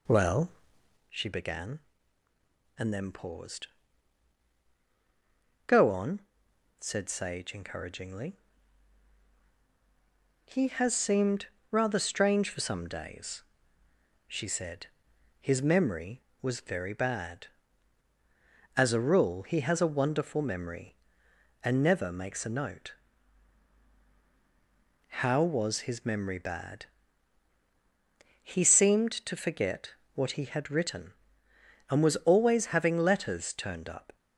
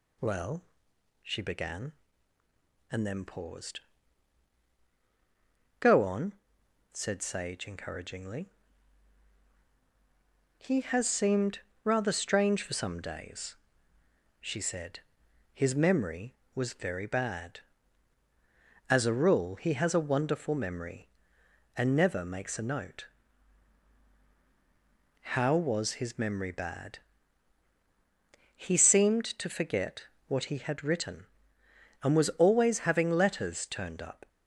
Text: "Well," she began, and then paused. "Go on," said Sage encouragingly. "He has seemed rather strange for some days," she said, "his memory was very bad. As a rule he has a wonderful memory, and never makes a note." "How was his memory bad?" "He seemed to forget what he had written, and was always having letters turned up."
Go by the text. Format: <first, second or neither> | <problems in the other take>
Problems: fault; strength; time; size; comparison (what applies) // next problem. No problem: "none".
second | starts louder than the rest; slight; until 1.2 s; 2 dB // pauses between "seemed" and "rather"; slight; at 11.4 s; 0.24 s long; slight in the second // pauses between "forget" and "what"; slight; at 29.9 s; 0.18 s long; slight in the second